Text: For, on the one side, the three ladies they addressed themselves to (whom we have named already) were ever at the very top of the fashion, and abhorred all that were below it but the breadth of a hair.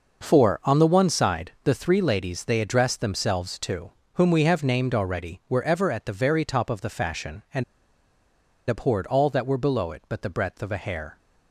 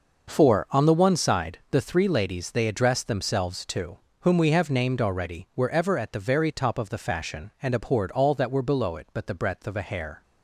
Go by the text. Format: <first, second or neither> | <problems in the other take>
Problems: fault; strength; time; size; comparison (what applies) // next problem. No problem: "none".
second | pauses between "and" and "abhorred"; at 7.6 s; 1.0 s long